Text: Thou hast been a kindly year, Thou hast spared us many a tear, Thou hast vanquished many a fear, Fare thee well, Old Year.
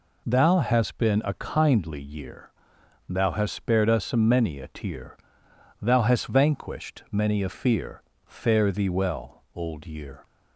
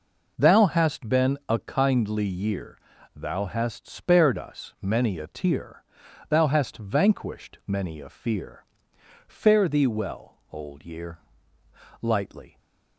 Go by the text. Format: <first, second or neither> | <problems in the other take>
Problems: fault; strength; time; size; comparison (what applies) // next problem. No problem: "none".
first | goes on to say "Lightly"; from 12.0 s on; 0.56 s long